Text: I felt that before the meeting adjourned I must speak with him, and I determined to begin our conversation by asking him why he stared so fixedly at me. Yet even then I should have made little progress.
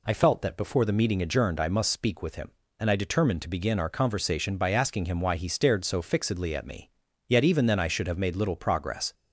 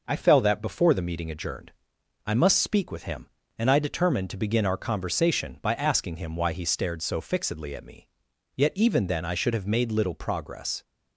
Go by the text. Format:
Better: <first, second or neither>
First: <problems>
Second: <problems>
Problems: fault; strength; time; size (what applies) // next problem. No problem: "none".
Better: first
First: none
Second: says "fell" for "felt"; at 0.1 s // pauses between "adjourned" and "I"; noticeable; at 1.7 s; 0.56 s long